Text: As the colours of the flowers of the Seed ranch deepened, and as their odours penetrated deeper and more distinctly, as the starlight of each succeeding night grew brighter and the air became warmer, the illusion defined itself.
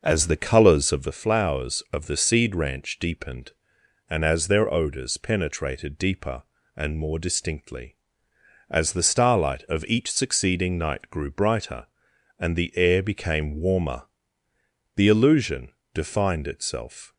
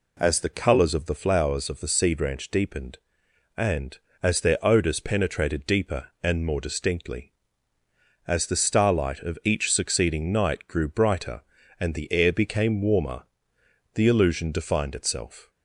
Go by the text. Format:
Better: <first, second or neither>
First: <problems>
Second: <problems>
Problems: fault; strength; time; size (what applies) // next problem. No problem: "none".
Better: second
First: starts louder than the rest; noticeable; until 1.2 s; 5.5 dB // pauses between "illusion" and "defined"; slight; at 15.7 s; 0.22 s long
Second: none